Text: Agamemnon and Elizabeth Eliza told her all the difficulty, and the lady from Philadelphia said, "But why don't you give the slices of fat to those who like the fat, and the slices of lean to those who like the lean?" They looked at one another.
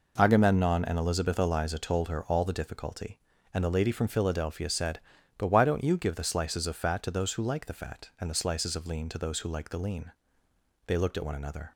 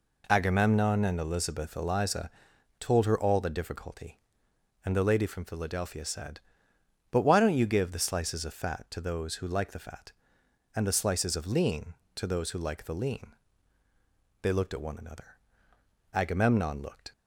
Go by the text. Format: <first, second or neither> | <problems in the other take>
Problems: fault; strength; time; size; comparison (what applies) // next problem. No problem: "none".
first | pauses between "Eliza" and "told"; noticeable; at 2.2 s; 0.50 s long // goes on to say "Agamemnon looked"; noticeable; from 16.1 s on; 0.98 s long